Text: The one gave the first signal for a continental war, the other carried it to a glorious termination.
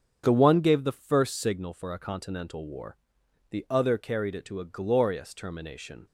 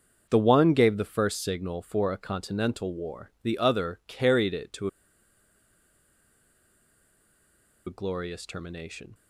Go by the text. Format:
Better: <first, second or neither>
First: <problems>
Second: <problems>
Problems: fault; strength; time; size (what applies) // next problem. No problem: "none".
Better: first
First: starts louder than the rest; strong; until 1.2 s; 7.5 dB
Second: starts louder than the rest; until 1.3 s; 6.5 dB // pauses between "to" and "a"; strong; at 4.8 s; 2.9 s long